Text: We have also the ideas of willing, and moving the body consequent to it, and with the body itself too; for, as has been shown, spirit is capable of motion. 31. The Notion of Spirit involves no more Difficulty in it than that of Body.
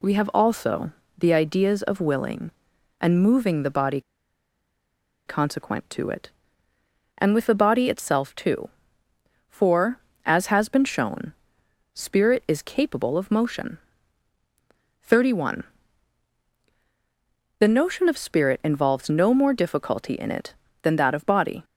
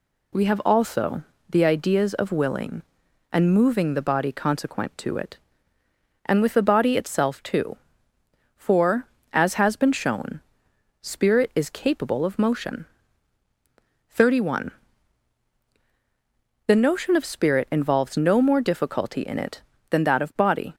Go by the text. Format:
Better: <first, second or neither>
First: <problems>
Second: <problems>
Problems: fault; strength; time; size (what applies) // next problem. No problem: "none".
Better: second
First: pauses between "also" and "the"; slight; at 0.9 s; 0.26 s long // pauses between "body" and "consequent"; strong; at 4.0 s; 1.2 s long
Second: pauses between "also" and "the"; slight; at 1.2 s; 0.26 s long